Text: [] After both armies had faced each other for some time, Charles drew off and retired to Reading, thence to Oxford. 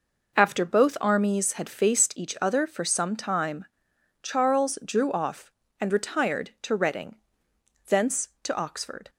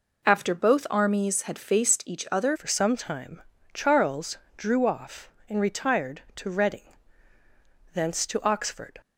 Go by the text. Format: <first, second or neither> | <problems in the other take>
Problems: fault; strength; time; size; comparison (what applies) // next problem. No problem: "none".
first | changes voice at "for"; from 2.5 s on; 6.5 s long // pauses between "Charles" and "drew"; slight; at 4.3 s; 0.20 s long